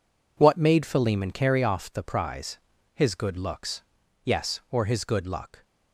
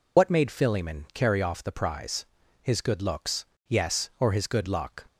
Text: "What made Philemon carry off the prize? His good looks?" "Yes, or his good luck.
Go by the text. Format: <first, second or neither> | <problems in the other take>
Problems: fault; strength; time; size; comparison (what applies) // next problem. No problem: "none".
first | loses the start of "What"; at 0.1 s; 70 ms